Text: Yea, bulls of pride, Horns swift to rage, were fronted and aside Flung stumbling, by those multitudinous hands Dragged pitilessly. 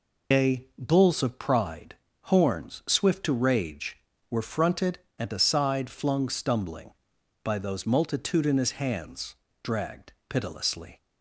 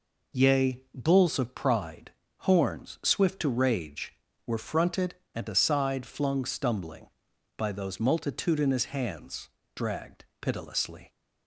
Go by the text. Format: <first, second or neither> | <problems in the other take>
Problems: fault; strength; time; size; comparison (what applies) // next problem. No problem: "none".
second | loses the start of "Yea"; at 0.3 s; 125 ms // pauses between "hands" and "Dragged"; slight; at 9.3 s; 0.26 s long; slight in the second // pauses between "Dragged" and "pitilessly"; slight; at 10.1 s; 0.16 s long; slight in the second